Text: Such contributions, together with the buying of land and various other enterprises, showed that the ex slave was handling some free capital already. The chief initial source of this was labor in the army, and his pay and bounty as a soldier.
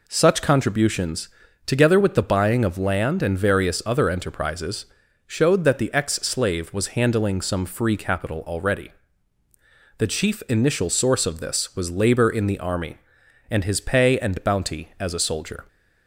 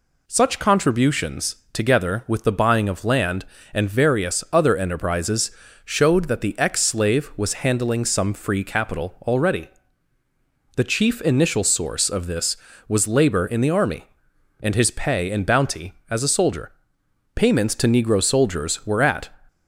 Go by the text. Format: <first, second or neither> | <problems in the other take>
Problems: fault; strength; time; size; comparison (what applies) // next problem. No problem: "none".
first | goes on to say "Payments to Negro soldiers were at"; strong; from 17.3 s on; 1.9 s long